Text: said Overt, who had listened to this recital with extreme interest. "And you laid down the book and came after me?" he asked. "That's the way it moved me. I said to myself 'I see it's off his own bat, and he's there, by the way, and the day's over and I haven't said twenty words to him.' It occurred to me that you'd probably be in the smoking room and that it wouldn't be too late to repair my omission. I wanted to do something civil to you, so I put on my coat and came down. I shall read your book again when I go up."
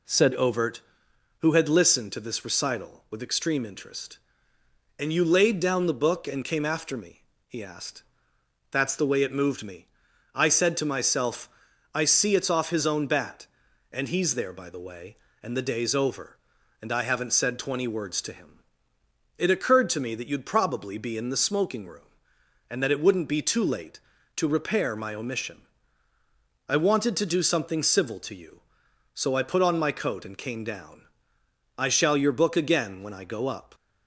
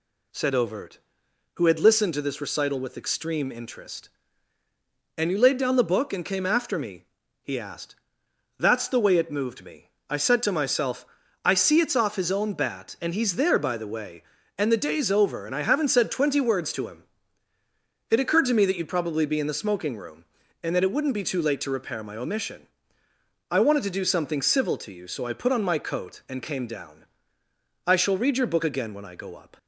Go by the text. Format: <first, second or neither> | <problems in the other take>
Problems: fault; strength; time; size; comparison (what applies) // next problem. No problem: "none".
second | pauses between "myself" and "I"; at 11.4 s; 0.44 s long; also in the second // skips "read"; at 32.1 s